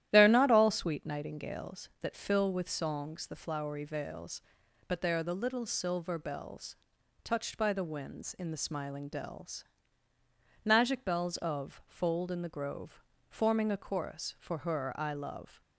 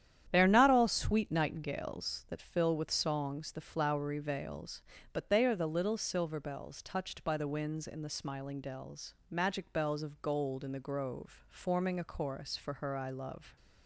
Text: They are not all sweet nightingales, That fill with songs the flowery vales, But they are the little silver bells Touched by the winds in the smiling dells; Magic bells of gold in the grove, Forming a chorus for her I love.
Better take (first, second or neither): second